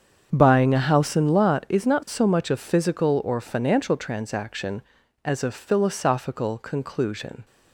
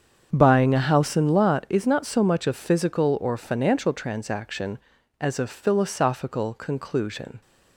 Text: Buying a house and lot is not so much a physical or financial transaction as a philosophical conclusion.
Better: neither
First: starts louder than the rest; strong; until 1.3 s; 7.5 dB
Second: starts louder than the rest; strong; until 1.3 s; 7.5 dB

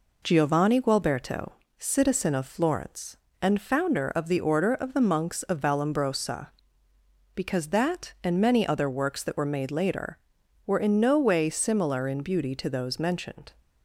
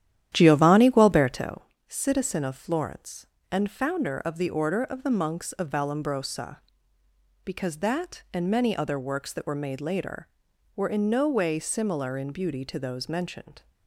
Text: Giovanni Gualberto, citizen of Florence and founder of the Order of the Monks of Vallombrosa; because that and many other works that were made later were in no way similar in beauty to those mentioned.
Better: first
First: none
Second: starts louder than the rest; strong; until 1.6 s; 11.5 dB

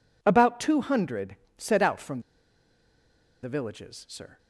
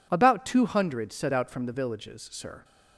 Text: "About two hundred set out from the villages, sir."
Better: second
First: pauses between "hundred" and "set"; slight; at 1.3 s; 0.22 s long // pauses between "from" and "the"; at 2.2 s; 1.2 s long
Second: none

